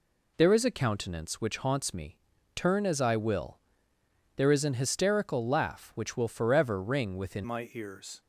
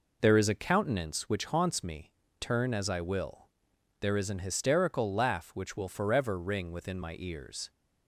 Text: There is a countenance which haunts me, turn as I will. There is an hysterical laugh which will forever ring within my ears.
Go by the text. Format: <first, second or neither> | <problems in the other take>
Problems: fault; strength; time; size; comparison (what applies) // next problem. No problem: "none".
second | changes voice at "my"; from 7.4 s on; 0.8 s long